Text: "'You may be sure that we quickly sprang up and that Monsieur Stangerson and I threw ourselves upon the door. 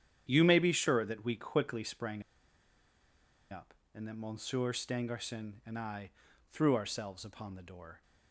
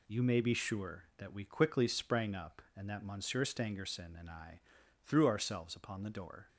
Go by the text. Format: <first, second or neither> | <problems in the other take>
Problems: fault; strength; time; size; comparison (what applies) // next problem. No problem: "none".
second | starts louder than the rest; strong; until 1.3 s; 9.5 dB // pauses between "sprang" and "up"; strong; at 2.2 s; 1.2 s long // pauses between "I" and "threw"; at 6.0 s; 0.42 s long; noticeable in the second